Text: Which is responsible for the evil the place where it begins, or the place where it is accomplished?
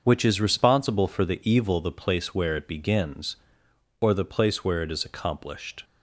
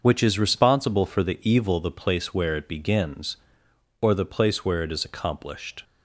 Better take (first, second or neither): neither